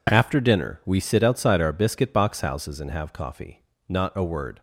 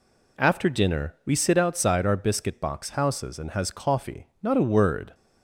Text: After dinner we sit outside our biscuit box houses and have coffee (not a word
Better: first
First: none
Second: says "has" for "have"; at 3.5 s

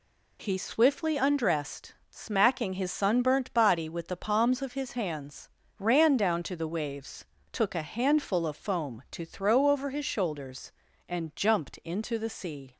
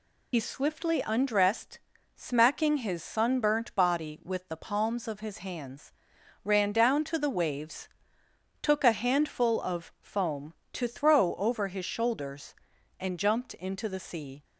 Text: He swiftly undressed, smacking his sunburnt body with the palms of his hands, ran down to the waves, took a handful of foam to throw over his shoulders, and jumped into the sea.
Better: first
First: none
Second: loses the start of "He"; at 0.3 s; 60 ms

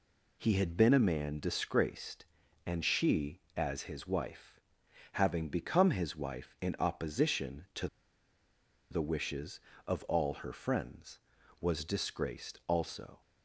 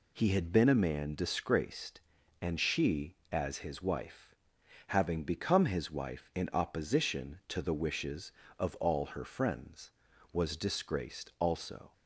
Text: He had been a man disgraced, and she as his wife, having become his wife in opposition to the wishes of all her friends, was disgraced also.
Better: second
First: pauses between "to" and "the"; at 7.8 s; 1.0 s long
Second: none

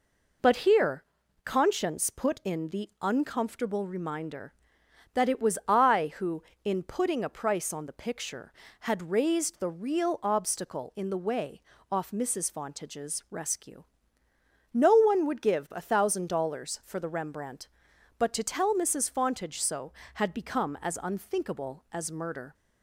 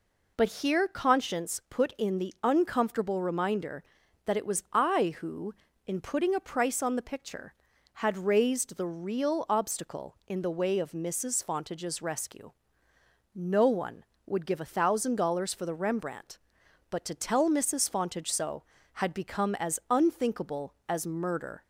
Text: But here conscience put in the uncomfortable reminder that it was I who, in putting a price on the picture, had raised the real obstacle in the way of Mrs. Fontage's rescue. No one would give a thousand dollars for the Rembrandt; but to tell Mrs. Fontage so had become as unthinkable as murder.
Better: second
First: pauses between "here" and "conscience"; at 1.0 s; 0.40 s long // says "off" for "of"; at 11.9 s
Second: none

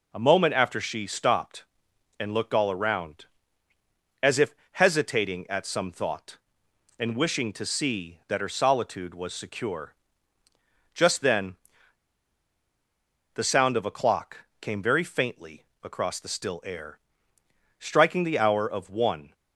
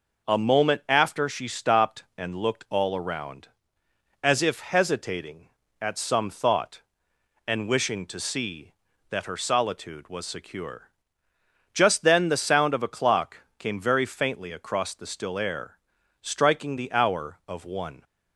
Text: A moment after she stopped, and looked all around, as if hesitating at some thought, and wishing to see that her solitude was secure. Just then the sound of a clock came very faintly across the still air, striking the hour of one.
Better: second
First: pauses between "if" and "hesitating"; slight; at 4.5 s; 0.18 s long // pauses between "then" and "the"; strong; at 11.5 s; 1.7 s long // pauses between "clock" and "came"; slight; at 14.4 s; 0.16 s long // pauses between "faintly" and "across"; slight; at 15.6 s; 0.18 s long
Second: pauses between "clock" and "came"; slight; at 13.3 s; 0.20 s long

